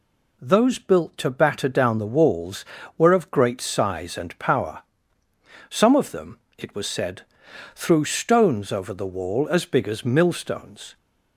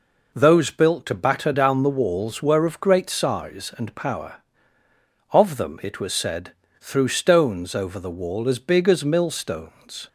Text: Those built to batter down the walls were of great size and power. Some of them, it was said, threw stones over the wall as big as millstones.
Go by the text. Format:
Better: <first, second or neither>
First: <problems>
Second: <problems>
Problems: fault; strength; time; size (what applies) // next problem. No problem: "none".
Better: first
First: none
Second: skips "Some"; at 4.8 s